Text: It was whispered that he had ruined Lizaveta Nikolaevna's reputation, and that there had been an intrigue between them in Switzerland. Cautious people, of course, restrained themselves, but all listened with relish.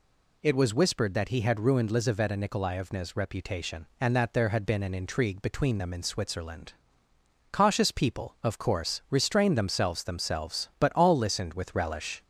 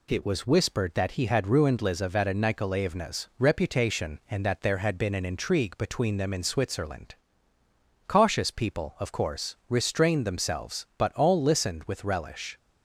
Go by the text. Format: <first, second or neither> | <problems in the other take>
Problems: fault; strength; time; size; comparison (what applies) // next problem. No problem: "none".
second | says "themselves" twice; at 10.0 s